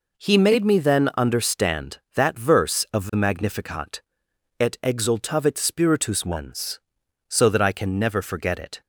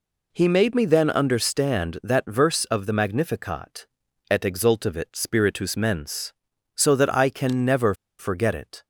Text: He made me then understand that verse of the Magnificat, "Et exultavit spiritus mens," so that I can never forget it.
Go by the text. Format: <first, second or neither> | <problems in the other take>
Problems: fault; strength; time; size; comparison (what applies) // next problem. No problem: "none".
first | pauses between "never" and "forget"; slight; at 7.9 s; 0.25 s long